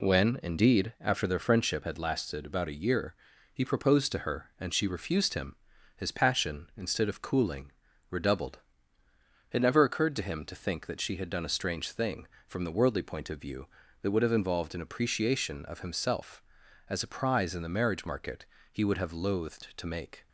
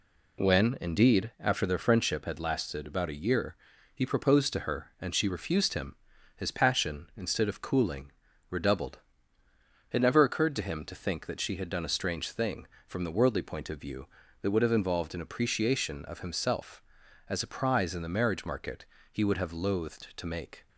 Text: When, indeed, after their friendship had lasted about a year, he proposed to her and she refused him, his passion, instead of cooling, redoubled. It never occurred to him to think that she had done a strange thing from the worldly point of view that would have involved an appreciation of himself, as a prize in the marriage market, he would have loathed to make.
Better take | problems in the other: neither | none

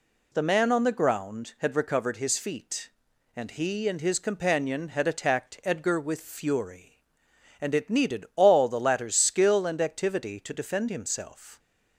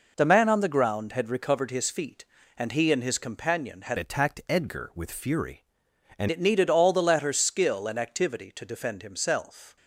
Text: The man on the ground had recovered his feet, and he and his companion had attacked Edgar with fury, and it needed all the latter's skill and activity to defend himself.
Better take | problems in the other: first | changes voice from "attacked" to "and"; from 3.9 to 6.2 s; 2.3 s long

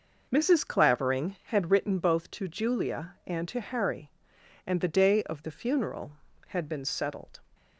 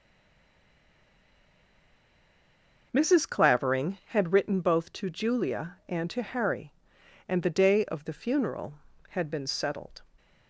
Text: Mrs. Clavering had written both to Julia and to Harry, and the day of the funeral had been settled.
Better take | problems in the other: first | stays silent before the first word; strong; until 2.9 s; 2.9 s long

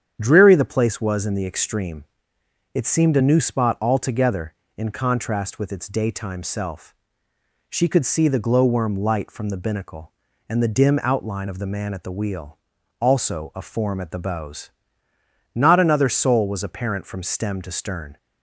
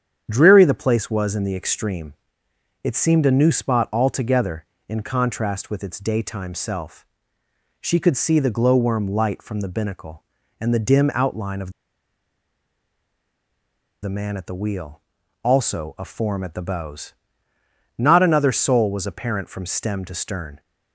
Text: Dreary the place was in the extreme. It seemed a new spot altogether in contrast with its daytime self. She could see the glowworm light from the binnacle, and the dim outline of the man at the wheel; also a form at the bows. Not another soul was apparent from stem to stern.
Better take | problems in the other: first | starts louder than the rest; strong; until 1.3 s; 8.5 dB; strong in the first // pauses between "of" and "the"; strong; at 11.7 s; 2.3 s long

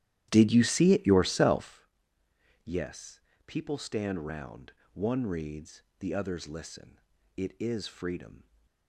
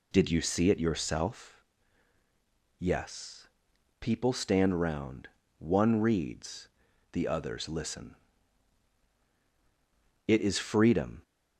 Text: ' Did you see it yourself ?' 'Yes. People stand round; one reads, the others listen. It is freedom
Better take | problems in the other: second | starts louder than the rest; strong; until 1.8 s; 12 dB

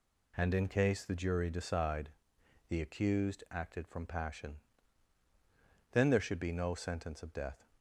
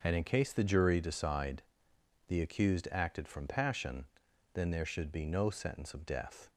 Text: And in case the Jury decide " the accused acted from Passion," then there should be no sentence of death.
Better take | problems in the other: neither | none

